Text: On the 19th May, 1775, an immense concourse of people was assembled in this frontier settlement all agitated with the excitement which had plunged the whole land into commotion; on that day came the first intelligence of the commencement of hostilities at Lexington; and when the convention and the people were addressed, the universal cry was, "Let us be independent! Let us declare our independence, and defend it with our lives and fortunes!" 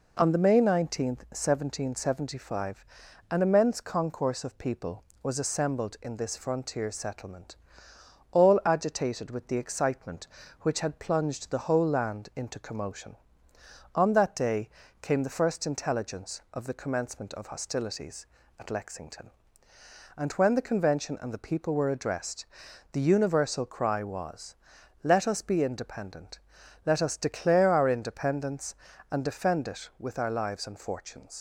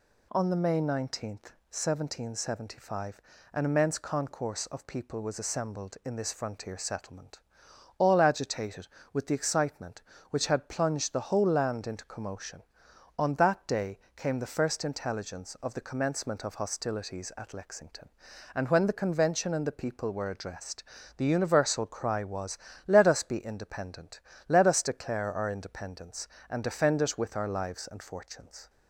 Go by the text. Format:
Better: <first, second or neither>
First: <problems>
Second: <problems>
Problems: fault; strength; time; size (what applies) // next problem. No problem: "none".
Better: second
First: pauses between "settlement" and "all"; noticeable; at 7.5 s; 0.78 s long // pauses between "day" and "came"; slight; at 14.6 s; 0.32 s long // leaves "fortunes" unfinished; at 31.3 s; 95 ms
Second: pauses between "settlement" and "all"; noticeable; at 7.3 s; 0.58 s long // pauses between "day" and "came"; slight; at 13.9 s; 0.18 s long